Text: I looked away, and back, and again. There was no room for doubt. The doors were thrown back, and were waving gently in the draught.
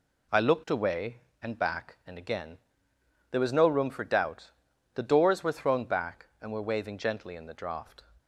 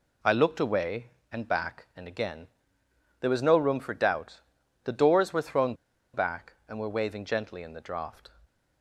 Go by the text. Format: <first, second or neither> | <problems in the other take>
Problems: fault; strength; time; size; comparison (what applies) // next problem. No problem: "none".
first | pauses between "thrown" and "back"; at 5.7 s; 0.40 s long